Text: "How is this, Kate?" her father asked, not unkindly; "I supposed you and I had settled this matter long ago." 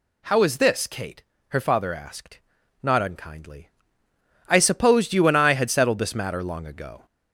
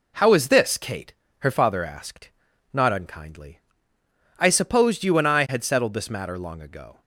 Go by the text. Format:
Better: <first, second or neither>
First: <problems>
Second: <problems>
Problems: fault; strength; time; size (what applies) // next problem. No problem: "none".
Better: second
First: gets louder; slight; throughout; 3 dB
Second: none